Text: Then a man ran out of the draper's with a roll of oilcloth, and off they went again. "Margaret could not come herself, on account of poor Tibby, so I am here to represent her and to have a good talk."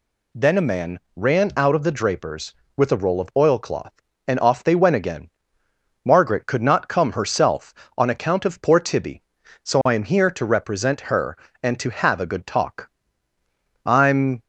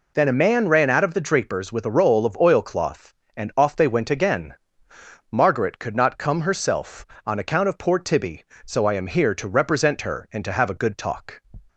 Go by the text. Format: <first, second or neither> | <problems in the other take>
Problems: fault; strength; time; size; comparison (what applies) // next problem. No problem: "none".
second | pauses between "man" and "ran"; slight; at 1.0 s; 0.16 s long // goes on to say "I'm"; from 13.8 s on; 0.56 s long